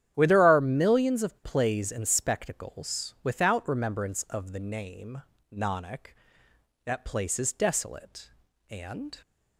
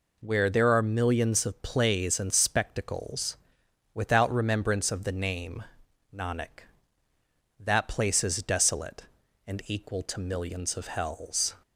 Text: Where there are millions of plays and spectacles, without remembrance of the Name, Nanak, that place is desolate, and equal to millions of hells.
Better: second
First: starts louder than the rest; strong; until 1.1 s; 10 dB // stops before "equal to millions of hells"; at 9.2 s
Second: none

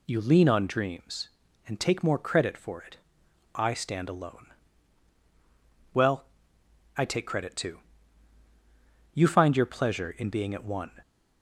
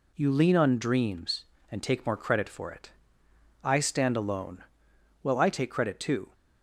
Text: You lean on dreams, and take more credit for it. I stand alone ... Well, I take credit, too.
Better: second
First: goes on to say "You find your pleasure in being at one"; strong; from 9.1 s on; 1.7 s long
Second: none

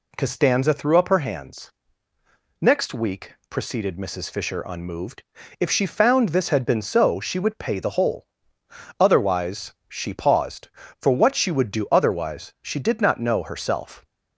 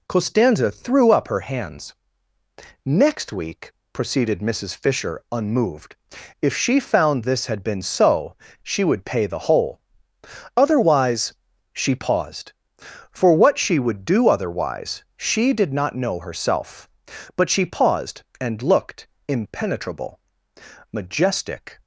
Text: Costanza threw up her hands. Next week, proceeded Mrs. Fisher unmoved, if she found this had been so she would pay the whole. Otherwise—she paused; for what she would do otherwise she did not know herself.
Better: first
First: none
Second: pauses between "so" and "she"; slight; at 8.3 s; 0.30 s long // goes on to say "But she paused and looked impenetrable majestic"; strong; from 17.3 s on; 4.4 s long

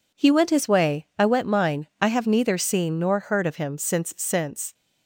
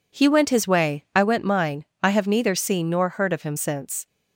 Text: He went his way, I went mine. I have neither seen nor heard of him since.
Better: second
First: says "since" twice; at 4.1 s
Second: none

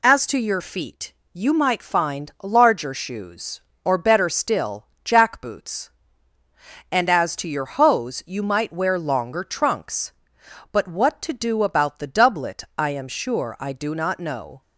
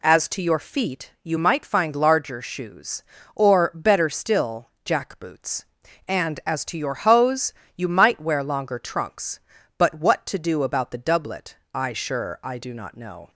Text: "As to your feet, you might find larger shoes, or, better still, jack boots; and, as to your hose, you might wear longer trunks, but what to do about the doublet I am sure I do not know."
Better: first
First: none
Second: pauses between "doublet" and "I"; slight; at 11.5 s; 0.18 s long // skips "am"; at 11.9 s

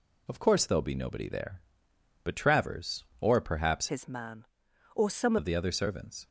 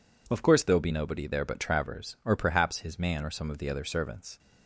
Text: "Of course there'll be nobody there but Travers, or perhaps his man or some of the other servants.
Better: second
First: changes voice from "his" to "some"; from 3.8 to 5.3 s; 1.5 s long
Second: none

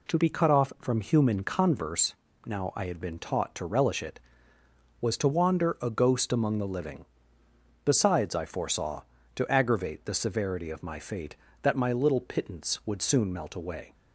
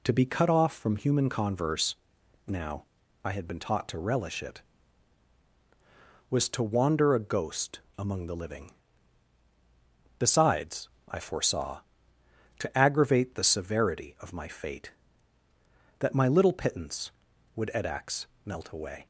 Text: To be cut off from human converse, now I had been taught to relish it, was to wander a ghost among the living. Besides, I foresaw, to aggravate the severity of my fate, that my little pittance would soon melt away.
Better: first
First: none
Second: pauses between "now" and "I"; at 2.8 s; 0.38 s long // pauses between "ghost" and "among"; slight; at 7.8 s; 0.18 s long // says "edax" for "soon"; at 17.7 s

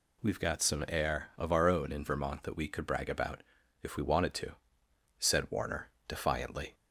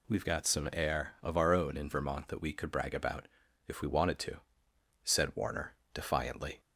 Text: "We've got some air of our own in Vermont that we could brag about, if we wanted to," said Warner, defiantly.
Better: neither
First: none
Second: none

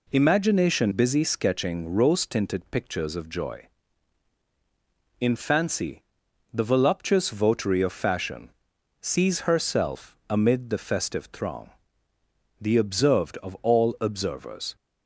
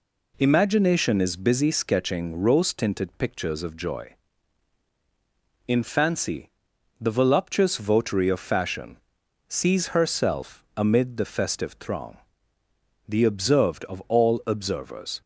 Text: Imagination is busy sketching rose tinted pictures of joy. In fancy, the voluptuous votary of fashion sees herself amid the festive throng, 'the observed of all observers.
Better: second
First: skips "is"; at 0.9 s // pauses between "fashion" and "sees"; noticeable; at 8.4 s; 0.50 s long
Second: pauses between "fashion" and "sees"; noticeable; at 8.9 s; 0.50 s long

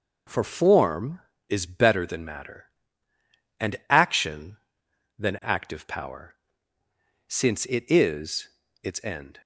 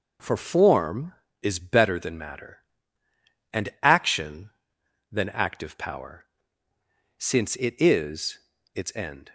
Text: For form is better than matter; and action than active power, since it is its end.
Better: neither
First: pauses between "is" and "its"; slight; at 8.4 s; 0.34 s long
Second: pauses between "is" and "its"; slight; at 8.3 s; 0.35 s long

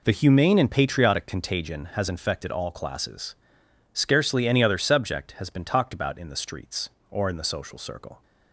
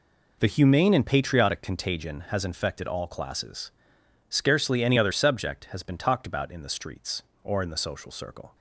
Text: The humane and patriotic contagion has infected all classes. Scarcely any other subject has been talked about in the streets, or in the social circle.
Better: neither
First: none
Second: none

